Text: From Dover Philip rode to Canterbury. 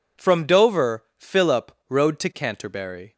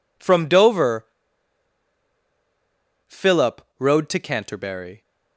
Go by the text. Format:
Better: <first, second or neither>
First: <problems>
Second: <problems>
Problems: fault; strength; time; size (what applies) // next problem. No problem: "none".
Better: first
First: pauses between "Philip" and "rode"; slight; at 1.7 s; 0.18 s long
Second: pauses between "Dover" and "Philip"; strong; at 1.0 s; 2.0 s long // pauses between "Philip" and "rode"; slight; at 3.6 s; 0.18 s long